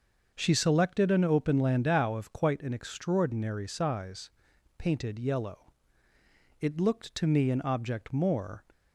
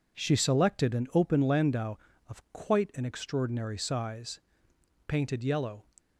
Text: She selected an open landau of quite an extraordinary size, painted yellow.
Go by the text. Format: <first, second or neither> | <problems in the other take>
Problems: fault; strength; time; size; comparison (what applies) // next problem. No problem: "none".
second | starts louder than the rest; until 1.3 s; 6.5 dB // goes on to say "It looked to me an object more"; strong; from 6.5 s on; 2.0 s long